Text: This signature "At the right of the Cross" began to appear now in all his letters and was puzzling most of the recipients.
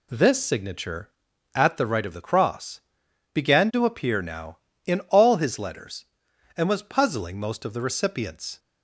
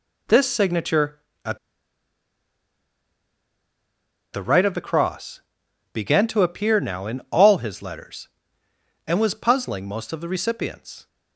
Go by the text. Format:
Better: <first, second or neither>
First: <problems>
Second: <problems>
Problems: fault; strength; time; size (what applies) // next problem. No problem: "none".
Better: first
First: pauses between "Cross" and "began"; noticeable; at 2.8 s; 0.54 s long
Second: pauses between "At" and "the"; strong; at 1.5 s; 2.7 s long // pauses between "Cross" and "began"; noticeable; at 5.3 s; 0.52 s long